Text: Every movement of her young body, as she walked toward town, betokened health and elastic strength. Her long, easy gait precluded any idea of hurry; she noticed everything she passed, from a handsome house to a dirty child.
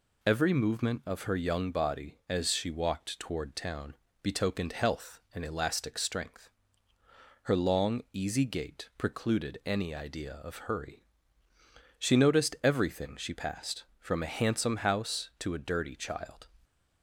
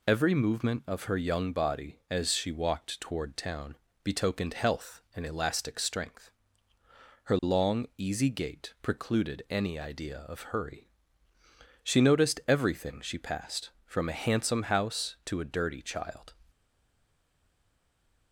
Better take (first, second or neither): first